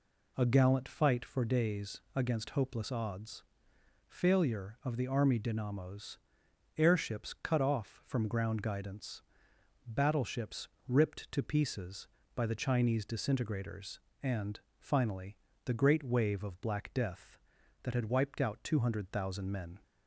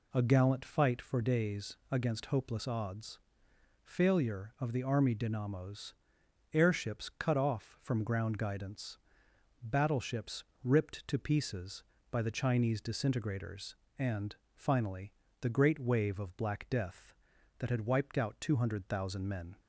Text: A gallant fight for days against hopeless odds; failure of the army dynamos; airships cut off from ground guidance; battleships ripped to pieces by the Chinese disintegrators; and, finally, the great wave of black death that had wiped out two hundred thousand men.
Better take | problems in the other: neither | pauses between "battleships" and "ripped"; slight; the same in both

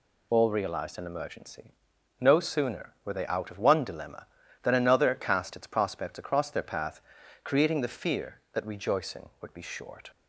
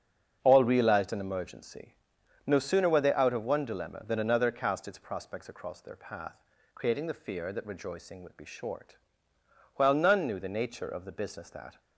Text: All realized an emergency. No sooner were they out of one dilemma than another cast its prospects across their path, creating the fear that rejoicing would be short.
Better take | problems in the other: first | starts louder than the rest; strong; until 1.4 s; 7.5 dB // goes on to say "While none knew the nature of the business that"; strong; from 9.7 s on; 2.0 s long

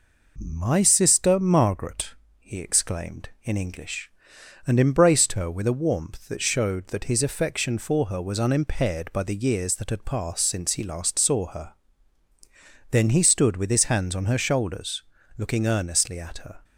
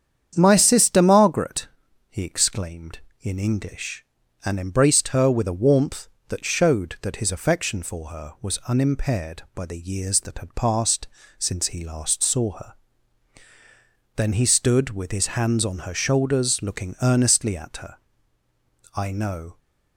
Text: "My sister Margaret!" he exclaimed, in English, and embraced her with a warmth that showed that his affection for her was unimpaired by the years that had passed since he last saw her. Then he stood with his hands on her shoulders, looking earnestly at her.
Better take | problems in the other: first | starts louder than the rest; strong; until 1.3 s; 8.5 dB // pauses between "passed" and "since"; slight; at 11.0 s; 0.32 s long // goes on to say "I know"; noticeable; from 18.9 s on; 0.62 s long

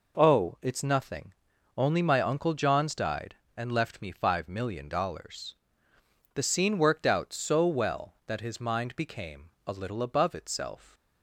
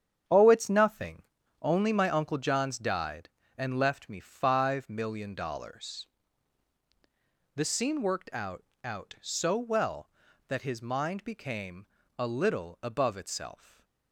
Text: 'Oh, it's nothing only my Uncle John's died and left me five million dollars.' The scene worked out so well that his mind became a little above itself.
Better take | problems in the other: first | starts louder than the rest; strong; until 1.6 s; 8.5 dB // pauses between "nothing" and "only"; at 1.2 s; 0.40 s long; also in the first // says "out" twice; at 8.8 s // pauses between "became" and "a"; slight; at 11.8 s; 0.32 s long; slight in the first // stays silent after the last word; slight; from 13.5 s on; 0.6 s long

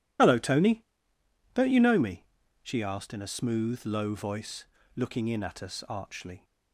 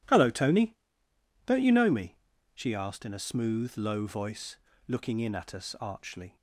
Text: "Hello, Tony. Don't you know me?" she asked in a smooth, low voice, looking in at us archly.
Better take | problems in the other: second | loses the start of "Hello"; at 0.1 s; 65 ms

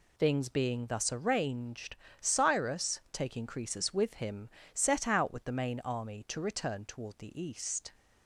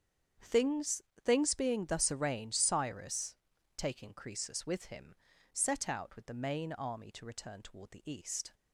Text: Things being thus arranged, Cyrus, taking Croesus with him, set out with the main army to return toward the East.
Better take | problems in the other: first | starts louder than the rest; strong; until 1.6 s; 8 dB // says "Things" twice; at 1.2 s

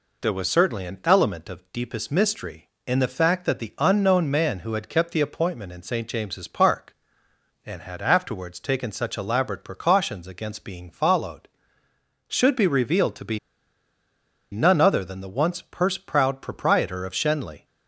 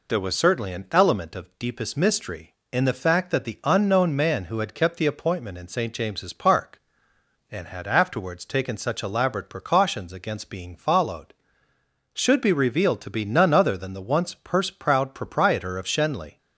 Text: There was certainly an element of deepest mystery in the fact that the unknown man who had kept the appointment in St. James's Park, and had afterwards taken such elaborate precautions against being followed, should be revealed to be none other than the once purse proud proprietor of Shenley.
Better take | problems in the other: second | pauses between "be" and "none"; at 13.3 s; 1.1 s long

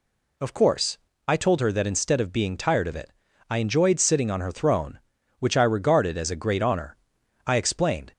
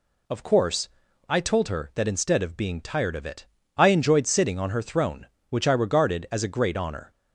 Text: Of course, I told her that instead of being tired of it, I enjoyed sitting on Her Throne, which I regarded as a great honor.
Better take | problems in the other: second | goes on to say "I explained"; noticeable; from 7.4 s on; 0.66 s long

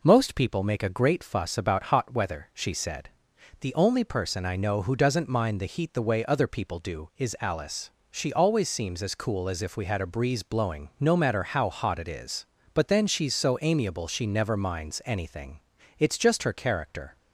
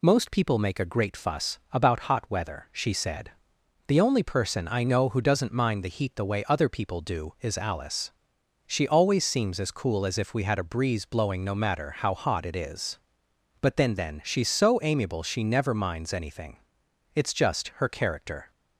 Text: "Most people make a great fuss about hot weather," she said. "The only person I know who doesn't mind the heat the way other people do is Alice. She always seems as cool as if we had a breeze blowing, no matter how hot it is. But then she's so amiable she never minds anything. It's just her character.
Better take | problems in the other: first | says "then" twice; at 13.9 s

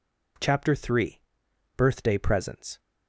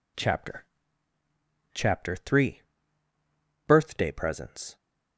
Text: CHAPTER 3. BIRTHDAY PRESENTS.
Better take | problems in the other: first | says "CHAPTER" twice; at 1.7 s

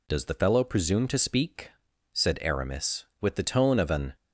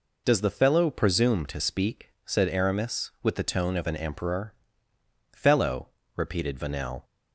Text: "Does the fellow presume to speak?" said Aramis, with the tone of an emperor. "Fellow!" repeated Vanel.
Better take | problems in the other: second | stops before "emperor Fellow repeated Vanel"; at 4.1 s

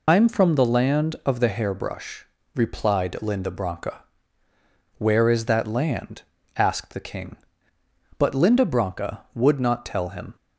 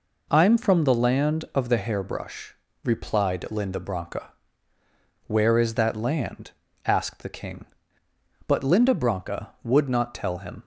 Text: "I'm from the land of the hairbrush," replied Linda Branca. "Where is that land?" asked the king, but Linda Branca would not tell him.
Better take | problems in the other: second | loses the start of "I'm"; at 0.0 s; 65 ms

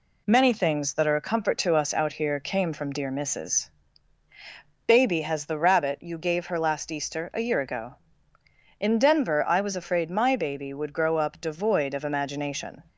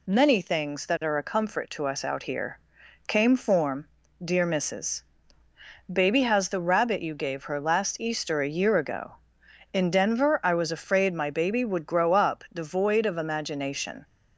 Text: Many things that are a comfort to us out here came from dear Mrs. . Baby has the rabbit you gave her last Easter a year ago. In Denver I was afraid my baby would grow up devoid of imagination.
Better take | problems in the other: first | pauses between "here" and "came"; noticeable; at 2.5 s; 0.50 s long // says "form" for "from"; at 3.3 s

